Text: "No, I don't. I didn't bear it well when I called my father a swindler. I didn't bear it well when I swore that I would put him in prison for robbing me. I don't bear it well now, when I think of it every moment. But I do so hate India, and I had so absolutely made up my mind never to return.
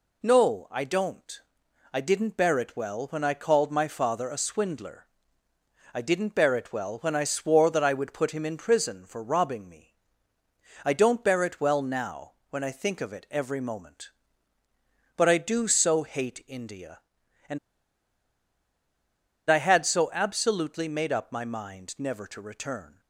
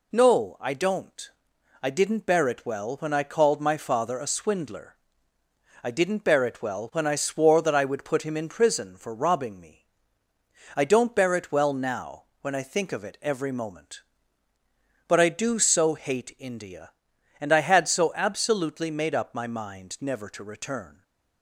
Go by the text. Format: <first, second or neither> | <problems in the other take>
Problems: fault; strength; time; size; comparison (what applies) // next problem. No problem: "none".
second | pauses between "and" and "I"; strong; at 17.5 s; 1.9 s long